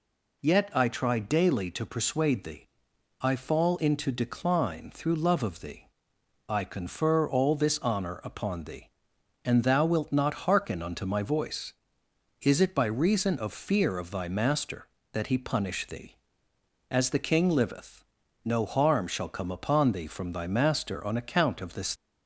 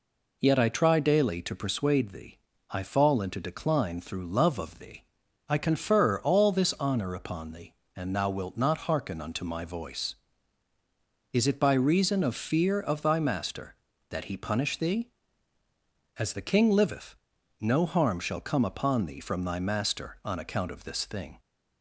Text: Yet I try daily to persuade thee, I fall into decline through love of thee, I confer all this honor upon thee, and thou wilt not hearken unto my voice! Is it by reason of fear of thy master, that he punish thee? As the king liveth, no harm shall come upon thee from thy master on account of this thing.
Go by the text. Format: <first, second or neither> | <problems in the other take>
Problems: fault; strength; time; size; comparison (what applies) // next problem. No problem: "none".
second | stops before "thing"; at 21.9 s